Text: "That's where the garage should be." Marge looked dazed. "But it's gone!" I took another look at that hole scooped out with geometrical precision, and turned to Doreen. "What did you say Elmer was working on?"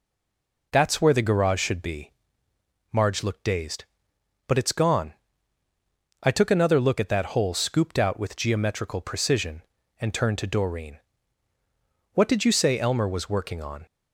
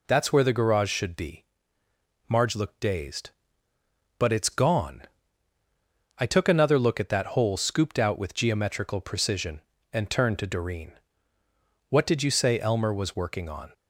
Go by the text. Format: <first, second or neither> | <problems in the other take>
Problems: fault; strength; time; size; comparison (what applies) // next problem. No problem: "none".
second | stays silent before the first word; slight; until 0.7 s; 0.7 s long